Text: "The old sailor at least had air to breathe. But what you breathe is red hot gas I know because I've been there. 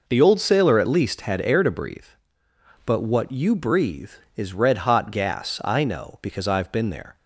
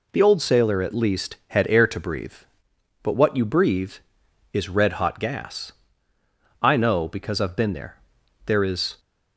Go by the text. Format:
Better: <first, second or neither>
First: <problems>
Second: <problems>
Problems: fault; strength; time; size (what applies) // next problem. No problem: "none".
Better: first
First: none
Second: pauses between "gas" and "I"; noticeable; at 5.7 s; 0.88 s long // goes on to say "There is"; from 8.4 s on; 0.54 s long